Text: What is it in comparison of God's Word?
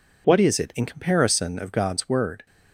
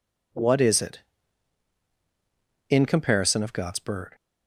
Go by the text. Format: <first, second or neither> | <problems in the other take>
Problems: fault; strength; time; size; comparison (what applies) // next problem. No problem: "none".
first | says "Bird" for "Word"; at 3.7 s